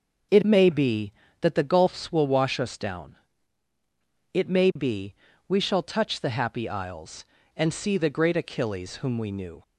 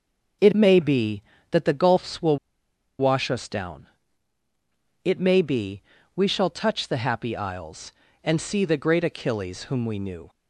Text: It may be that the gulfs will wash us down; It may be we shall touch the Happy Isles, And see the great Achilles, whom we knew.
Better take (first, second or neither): first